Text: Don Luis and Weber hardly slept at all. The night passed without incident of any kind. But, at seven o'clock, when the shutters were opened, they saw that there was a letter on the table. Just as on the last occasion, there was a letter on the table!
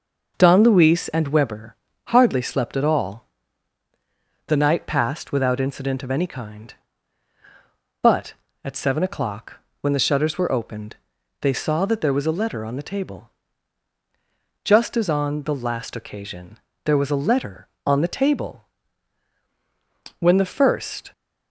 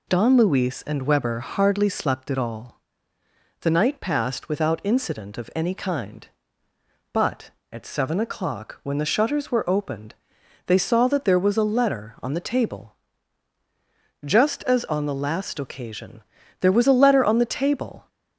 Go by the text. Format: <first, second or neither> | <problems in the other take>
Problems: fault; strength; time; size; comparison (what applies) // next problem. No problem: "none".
second | pauses between "Weber" and "hardly"; slight; at 1.7 s; 0.32 s long // goes on to say "When the first"; noticeable; from 20.1 s on; 0.94 s long